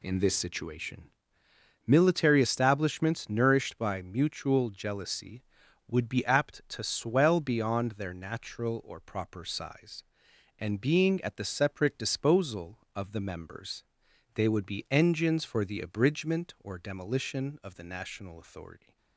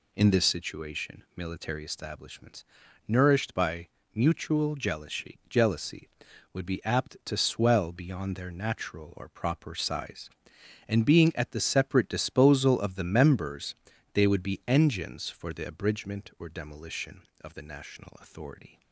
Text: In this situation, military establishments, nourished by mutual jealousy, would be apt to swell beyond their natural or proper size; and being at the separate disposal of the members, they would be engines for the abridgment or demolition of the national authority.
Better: first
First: none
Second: pauses between "by" and "mutual"; slight; at 3.8 s; 0.26 s long // says "jealousy" twice; at 5.4 s

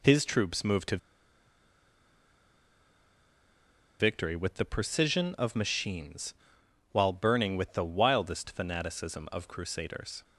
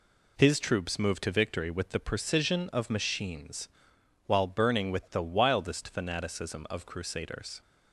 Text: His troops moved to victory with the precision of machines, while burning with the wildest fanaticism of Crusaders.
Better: second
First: pauses between "to" and "victory"; strong; at 0.9 s; 3.0 s long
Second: none

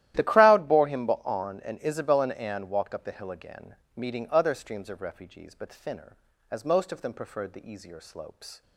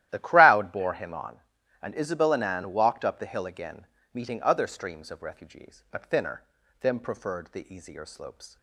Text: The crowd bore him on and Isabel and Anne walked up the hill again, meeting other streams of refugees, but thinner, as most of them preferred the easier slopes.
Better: first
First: starts louder than the rest; strong; until 1.1 s; 13.5 dB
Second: starts louder than the rest; strong; until 1.1 s; 13.5 dB // skips "as most of"; at 6.6 s

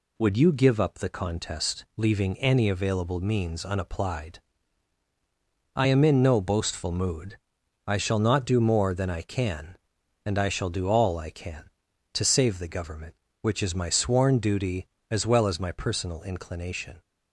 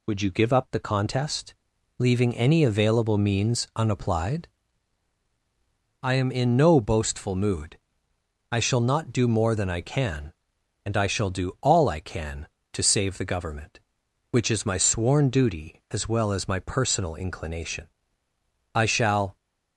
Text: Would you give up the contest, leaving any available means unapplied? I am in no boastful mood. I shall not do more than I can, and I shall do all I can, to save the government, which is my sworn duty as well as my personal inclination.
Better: first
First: none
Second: goes on to say "I shall"; noticeable; from 18.7 s on; 0.62 s long

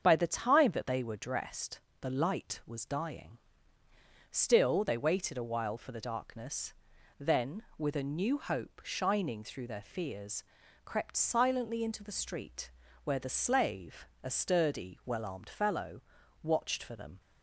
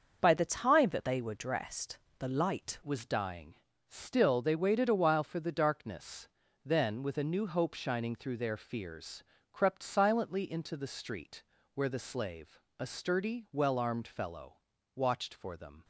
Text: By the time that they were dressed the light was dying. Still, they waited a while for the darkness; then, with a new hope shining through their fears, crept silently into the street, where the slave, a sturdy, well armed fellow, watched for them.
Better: first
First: starts louder than the rest; strong; until 1.0 s; 7 dB // pauses between "dressed" and "the"; slight; at 1.7 s; 0.20 s long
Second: starts louder than the rest; until 1.2 s; 6.5 dB // pauses between "dressed" and "the"; slight; at 1.9 s; 0.20 s long // changes voice at "was"; from 2.8 s on; 13.0 s long

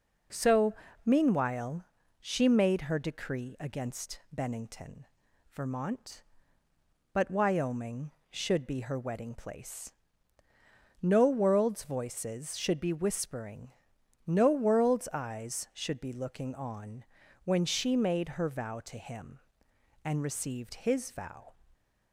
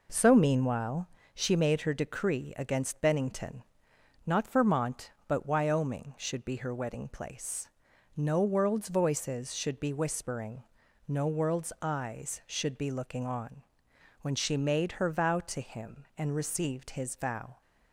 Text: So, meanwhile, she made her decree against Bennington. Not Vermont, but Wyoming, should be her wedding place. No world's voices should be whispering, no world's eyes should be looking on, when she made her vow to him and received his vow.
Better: second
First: skips "Not"; at 5.2 s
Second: none

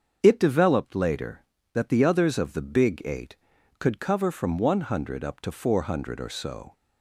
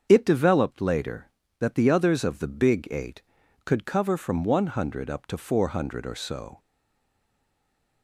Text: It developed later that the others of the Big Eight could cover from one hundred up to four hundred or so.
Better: first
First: starts louder than the rest; until 1.2 s; 7 dB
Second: starts louder than the rest; strong; until 1.0 s; 7 dB // stays silent after the last word; noticeable; from 6.5 s on; 1.5 s long

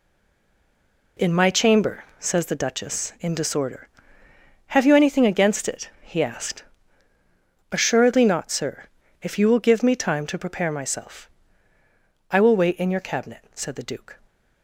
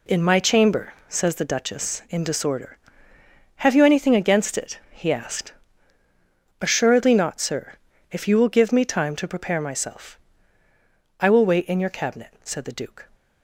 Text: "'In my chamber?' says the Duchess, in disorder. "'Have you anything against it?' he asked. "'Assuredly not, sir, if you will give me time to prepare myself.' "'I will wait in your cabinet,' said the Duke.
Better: second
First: stays silent before the first word; noticeable; until 1.1 s; 1.1 s long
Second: none

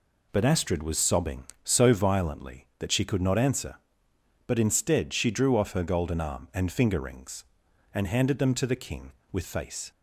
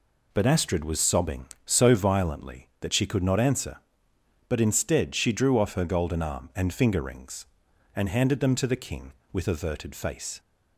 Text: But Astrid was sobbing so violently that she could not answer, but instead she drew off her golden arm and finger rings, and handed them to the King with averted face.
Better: second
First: skips "averted"; at 9.4 s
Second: none

